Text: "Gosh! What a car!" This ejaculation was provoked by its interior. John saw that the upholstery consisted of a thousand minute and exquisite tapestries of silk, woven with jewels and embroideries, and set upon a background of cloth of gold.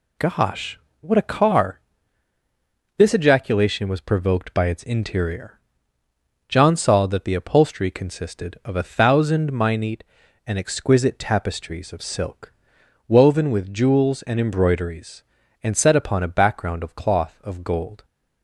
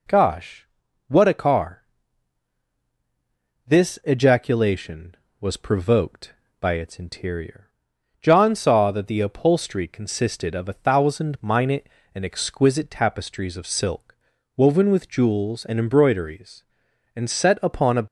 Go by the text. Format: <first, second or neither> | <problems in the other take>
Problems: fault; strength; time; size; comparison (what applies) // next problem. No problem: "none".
first | stops before "background of cloth of gold"; at 18.0 s